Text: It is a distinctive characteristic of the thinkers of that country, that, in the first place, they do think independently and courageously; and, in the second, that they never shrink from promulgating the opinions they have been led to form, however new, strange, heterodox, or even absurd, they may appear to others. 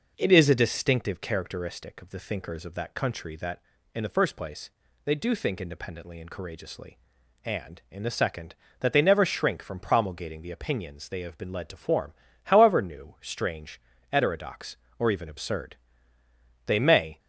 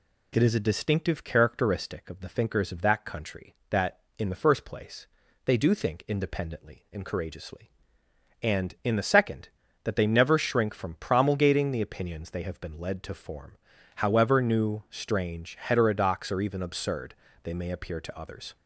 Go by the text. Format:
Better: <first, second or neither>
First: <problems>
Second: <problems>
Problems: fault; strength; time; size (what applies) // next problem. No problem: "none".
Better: second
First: stops before "appear to others"; at 17.1 s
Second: none